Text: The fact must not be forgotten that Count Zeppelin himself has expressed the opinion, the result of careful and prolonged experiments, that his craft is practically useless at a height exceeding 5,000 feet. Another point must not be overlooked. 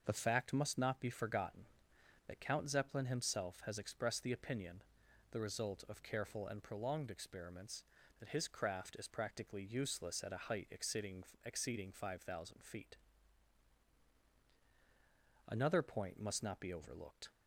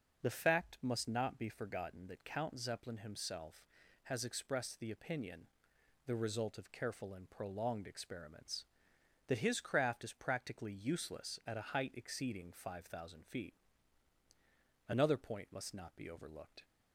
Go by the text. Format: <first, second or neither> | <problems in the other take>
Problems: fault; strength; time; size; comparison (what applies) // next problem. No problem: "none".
second | starts louder than the rest; until 1.0 s; 6 dB // says "exceeding" twice; at 11.4 s